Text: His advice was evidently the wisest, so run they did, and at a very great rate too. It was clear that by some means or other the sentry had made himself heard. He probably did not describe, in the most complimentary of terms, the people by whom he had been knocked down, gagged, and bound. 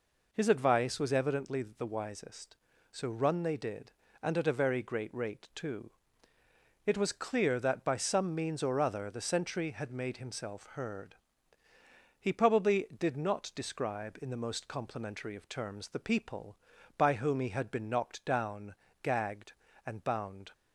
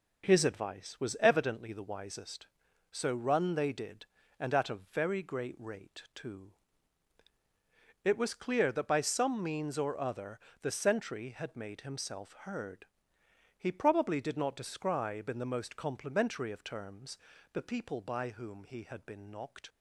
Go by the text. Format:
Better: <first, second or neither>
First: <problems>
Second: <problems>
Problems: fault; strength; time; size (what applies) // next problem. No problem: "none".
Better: first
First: none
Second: pauses between "other" and "the"; slight; at 10.3 s; 0.24 s long // stops before "down gagged and bound"; at 19.6 s